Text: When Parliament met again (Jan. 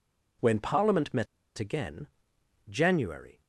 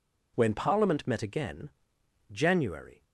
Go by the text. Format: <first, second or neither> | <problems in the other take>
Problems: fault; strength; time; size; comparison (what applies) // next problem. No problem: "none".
second | pauses between "met" and "again"; slight; at 1.2 s; 0.34 s long